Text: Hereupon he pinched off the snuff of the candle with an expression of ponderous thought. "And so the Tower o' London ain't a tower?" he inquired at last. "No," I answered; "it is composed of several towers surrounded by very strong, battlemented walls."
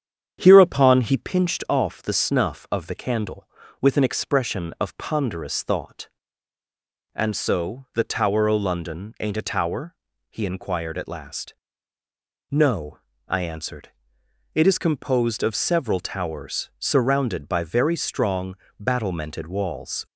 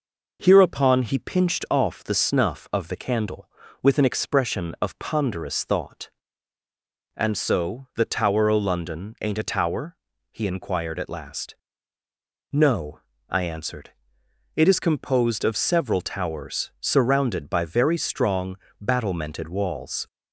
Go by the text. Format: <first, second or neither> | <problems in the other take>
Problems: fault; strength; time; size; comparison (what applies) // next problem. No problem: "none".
second | starts louder than the rest; strong; until 1.3 s; 8.5 dB